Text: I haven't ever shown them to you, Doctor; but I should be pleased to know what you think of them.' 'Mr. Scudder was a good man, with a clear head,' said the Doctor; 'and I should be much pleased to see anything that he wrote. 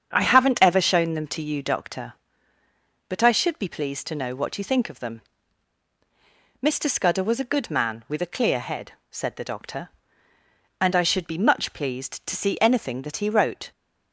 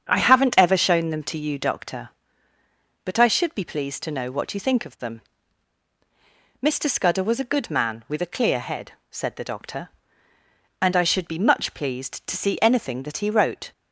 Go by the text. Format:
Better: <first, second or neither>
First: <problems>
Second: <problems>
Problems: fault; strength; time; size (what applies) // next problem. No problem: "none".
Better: neither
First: starts louder than the rest; strong; until 1.1 s; 7.5 dB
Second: starts louder than the rest; strong; until 1.1 s; 7.5 dB